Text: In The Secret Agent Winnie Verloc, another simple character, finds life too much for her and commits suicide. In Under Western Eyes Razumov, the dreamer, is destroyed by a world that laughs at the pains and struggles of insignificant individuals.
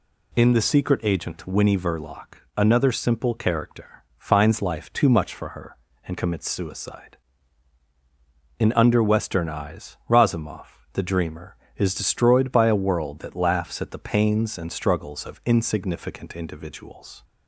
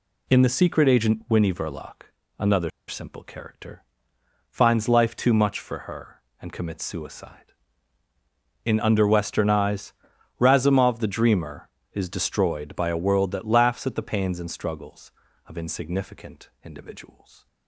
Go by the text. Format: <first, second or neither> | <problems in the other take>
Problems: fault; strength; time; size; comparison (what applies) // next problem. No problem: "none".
first | pauses between "another" and "simple"; slight; at 2.6 s; 0.19 s long // pauses between "Eyes" and "Razumov"; noticeable; at 9.9 s; 0.46 s long